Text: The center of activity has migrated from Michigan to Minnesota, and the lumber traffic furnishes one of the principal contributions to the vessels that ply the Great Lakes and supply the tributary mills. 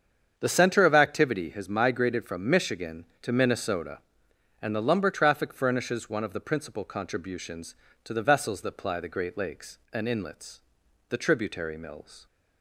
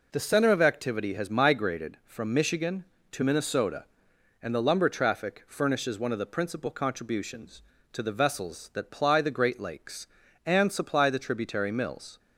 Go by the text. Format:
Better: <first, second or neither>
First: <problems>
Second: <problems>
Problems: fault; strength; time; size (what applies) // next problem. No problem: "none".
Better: second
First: starts louder than the rest; strong; until 1.3 s; 7.5 dB // says "inlets" for "supply"; at 10.0 s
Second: none